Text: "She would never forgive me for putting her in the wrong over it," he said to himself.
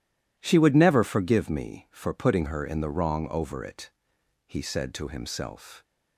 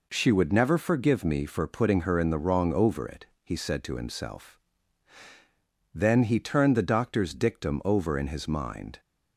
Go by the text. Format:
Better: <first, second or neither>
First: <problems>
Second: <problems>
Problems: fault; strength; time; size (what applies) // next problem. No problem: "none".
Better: first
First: none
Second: goes on to say "Then he turned the doctor's dictum over in his mind"; strong; from 5.9 s on; 3.0 s long